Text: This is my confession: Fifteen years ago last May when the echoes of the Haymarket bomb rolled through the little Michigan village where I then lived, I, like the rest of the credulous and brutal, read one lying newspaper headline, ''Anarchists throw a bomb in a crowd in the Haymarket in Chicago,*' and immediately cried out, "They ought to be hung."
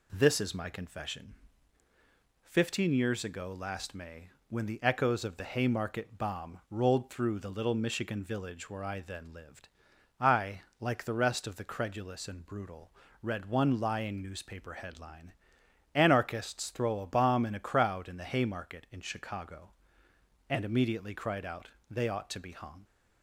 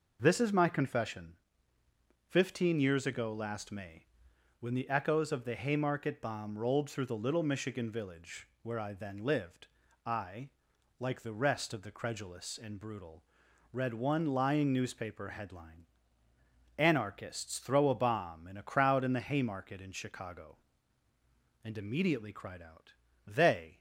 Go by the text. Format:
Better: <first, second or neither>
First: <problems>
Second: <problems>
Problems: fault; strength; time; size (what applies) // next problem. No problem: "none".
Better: first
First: pauses between "May" and "when"; slight; at 4.2 s; 0.22 s long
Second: pauses between "May" and "when"; noticeable; at 4.0 s; 0.54 s long // stops before "ought to be hung"; at 23.7 s